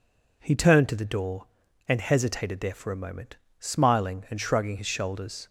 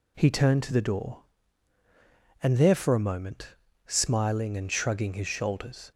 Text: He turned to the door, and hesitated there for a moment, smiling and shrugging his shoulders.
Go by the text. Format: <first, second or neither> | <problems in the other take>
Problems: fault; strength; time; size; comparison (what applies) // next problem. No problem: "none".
first | skips "hesitated"; at 2.5 s